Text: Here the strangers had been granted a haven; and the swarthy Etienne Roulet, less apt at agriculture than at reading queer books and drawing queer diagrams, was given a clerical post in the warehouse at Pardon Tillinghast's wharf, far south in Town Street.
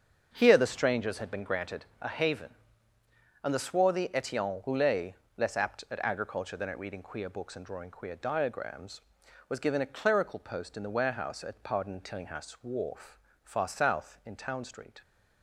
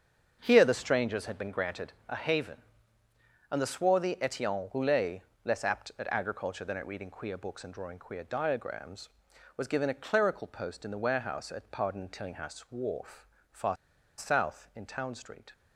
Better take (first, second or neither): first